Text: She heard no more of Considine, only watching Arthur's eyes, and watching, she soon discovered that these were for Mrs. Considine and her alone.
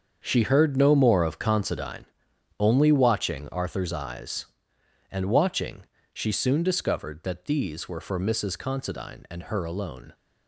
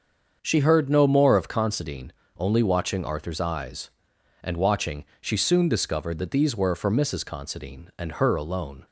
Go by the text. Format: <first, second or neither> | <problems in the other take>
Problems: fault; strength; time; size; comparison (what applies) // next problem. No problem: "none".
second | gets quieter; strong; throughout; 11.5 dB // starts louder than the rest; until 1.2 s; 7 dB; also in the second